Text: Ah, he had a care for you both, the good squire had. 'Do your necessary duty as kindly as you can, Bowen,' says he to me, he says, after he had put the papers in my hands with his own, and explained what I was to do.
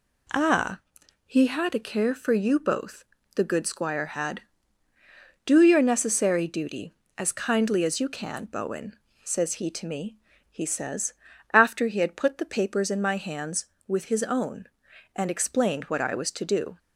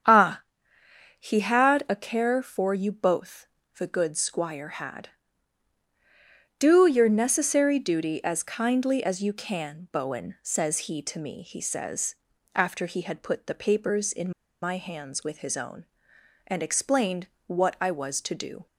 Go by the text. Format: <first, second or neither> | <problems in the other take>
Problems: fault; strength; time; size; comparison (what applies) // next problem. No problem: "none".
first | starts louder than the rest; strong; until 1.9 s; 8 dB // pauses between "in" and "my"; slight; at 14.3 s; 0.31 s long // pauses between "explained" and "what"; slight; at 17.2 s; 0.22 s long